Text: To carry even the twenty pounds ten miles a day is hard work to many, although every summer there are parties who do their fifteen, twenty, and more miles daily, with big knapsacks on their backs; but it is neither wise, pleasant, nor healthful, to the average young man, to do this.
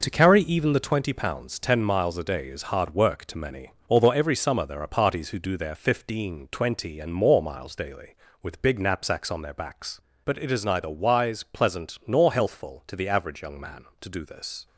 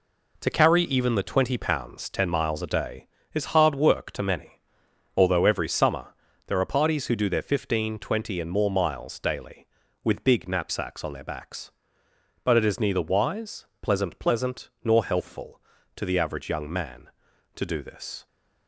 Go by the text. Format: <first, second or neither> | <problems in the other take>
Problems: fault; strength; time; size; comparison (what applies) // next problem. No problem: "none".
first | pauses between "summer" and "there"; slight; at 6.1 s; 0.32 s long // says "pleasant" twice; at 14.1 s